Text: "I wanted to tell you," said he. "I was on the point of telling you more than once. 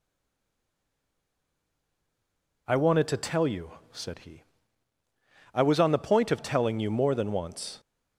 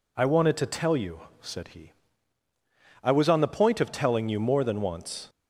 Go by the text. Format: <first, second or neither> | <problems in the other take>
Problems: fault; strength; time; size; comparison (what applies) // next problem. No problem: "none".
second | stays silent before the first word; strong; until 2.6 s; 2.6 s long